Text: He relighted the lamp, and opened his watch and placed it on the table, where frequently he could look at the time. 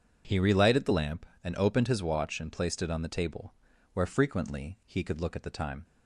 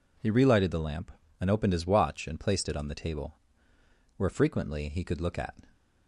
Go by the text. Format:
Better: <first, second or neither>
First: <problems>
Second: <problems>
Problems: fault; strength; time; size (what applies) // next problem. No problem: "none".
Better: first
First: none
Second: stops before "the time"; at 5.7 s